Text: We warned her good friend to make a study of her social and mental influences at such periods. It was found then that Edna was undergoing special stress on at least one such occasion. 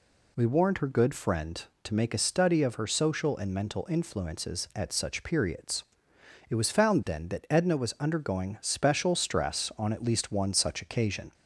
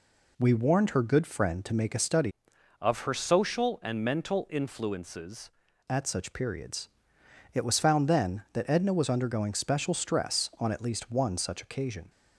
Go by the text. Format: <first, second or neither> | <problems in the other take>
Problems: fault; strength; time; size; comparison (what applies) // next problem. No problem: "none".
first | changes voice from "of" to "influences"; from 2.8 to 5.5 s; 2.7 s long